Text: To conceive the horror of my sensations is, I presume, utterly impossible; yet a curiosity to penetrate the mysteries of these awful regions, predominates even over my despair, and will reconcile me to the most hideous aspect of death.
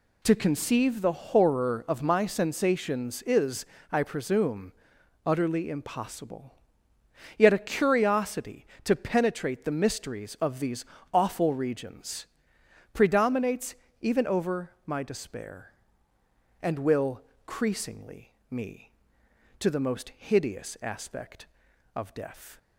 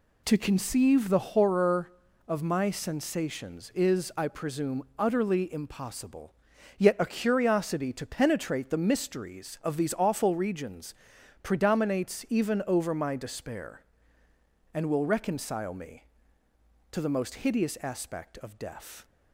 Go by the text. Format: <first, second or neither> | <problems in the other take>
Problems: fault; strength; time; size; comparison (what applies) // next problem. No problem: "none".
second | pauses between "these" and "awful"; slight; at 10.8 s; 0.30 s long // pauses between "predominates" and "even"; slight; at 13.7 s; 0.26 s long // pauses between "over" and "my"; slight; at 14.6 s; 0.16 s long // says "creasingly" for "reconcile"; at 17.4 s